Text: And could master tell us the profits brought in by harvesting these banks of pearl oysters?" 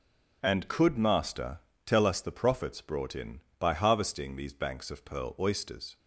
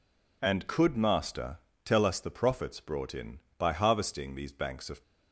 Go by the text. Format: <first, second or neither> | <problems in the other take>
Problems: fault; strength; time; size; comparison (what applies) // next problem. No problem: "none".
first | pauses between "master" and "tell"; slight; at 1.5 s; 0.28 s long; slight in the first // stops before "pearl oysters"; at 5.0 s